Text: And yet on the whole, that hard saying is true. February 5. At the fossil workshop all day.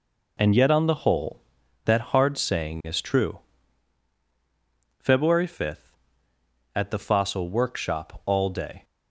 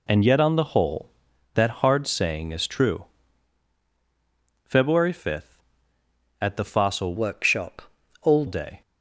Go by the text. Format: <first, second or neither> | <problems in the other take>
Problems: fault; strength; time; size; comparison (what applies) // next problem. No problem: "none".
first | changes voice from "workshop" to "all"; from 7.1 to 8.4 s; 1.3 s long // pauses between "workshop" and "all"; at 7.8 s; 0.40 s long